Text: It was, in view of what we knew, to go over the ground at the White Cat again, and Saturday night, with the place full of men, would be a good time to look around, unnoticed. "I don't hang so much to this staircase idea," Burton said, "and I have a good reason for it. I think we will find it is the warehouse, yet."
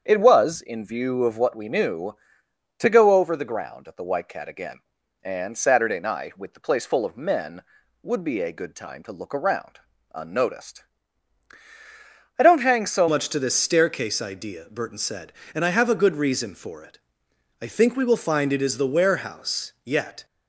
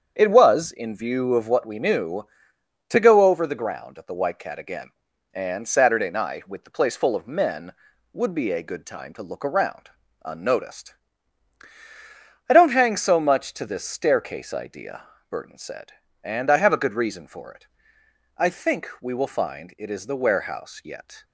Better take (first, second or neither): second